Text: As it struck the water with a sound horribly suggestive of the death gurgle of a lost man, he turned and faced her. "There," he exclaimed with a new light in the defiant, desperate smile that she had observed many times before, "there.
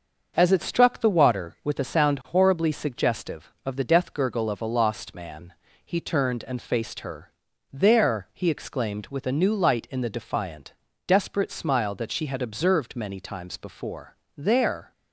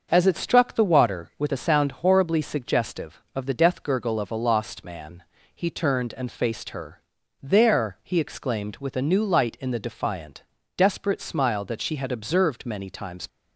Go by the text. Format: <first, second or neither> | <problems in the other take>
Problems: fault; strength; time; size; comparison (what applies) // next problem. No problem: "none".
first | starts louder than the rest; until 1.1 s; 6.5 dB; also in the first // stops before "before there"; at 13.2 s